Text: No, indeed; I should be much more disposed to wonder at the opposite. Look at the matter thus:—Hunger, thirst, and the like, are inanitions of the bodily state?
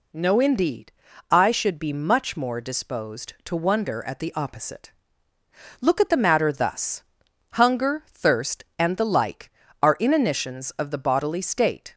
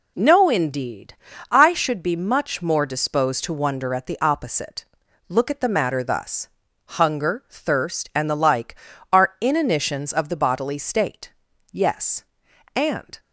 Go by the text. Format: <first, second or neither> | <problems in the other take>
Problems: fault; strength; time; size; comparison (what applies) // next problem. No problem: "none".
first | goes on to say "Yes And"; from 11.7 s on; 1.4 s long